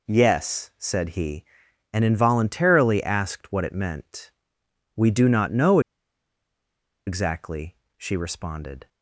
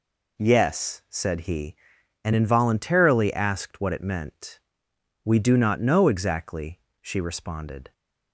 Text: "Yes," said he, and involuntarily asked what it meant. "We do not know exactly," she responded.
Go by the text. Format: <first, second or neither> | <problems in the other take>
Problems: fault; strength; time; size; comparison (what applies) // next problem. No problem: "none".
second | pauses between "know" and "exactly"; strong; at 5.7 s; 1.2 s long